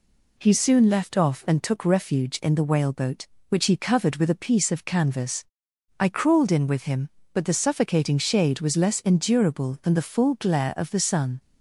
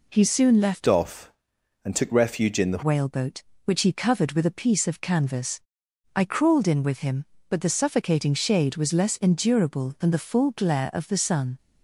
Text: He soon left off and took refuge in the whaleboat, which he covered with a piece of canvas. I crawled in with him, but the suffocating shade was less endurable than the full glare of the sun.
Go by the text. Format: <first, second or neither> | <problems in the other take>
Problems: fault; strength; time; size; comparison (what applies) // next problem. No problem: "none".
first | changes voice from "off" to "the"; from 0.8 to 2.8 s; 2.0 s long